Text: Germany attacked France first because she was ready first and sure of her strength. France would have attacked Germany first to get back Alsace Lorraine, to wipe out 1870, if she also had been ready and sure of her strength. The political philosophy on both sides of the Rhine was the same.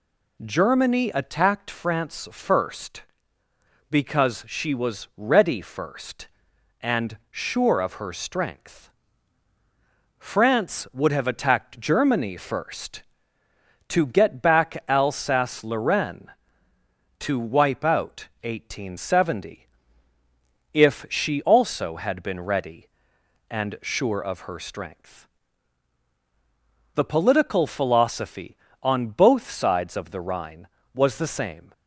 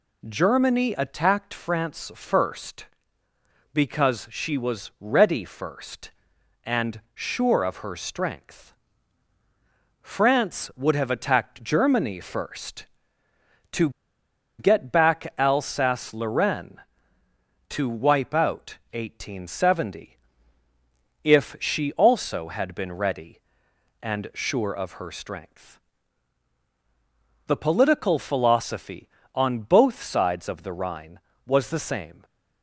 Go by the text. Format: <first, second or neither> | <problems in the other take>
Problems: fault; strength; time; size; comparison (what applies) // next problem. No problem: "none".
first | pauses between "to" and "get"; noticeable; at 13.8 s; 0.68 s long